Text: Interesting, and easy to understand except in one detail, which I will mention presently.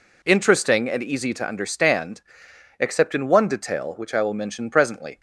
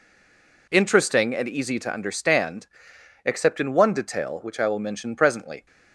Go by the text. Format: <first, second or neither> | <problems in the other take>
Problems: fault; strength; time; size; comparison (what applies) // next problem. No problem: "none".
first | stays silent before the first word; slight; until 0.6 s; 0.6 s long // pauses between "understand" and "except"; noticeable; at 2.6 s; 0.58 s long; noticeable in the first